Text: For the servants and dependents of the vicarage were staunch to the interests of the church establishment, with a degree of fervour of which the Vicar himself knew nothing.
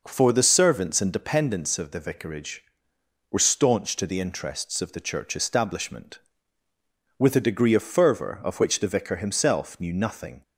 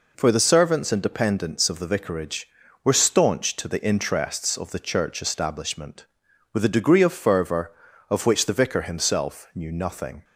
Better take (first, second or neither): neither